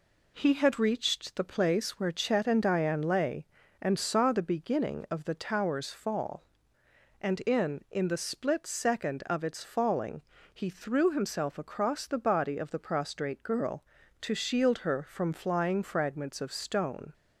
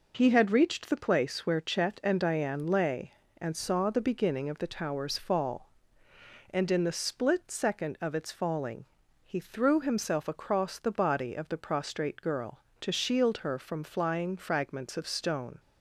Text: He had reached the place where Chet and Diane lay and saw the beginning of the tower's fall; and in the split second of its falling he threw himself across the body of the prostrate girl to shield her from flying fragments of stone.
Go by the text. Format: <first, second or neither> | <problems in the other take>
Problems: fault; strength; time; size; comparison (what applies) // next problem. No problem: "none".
second | says "in" twice; at 7.8 s // pauses between "falling" and "he"; slight; at 10.2 s; 0.30 s long; also in the second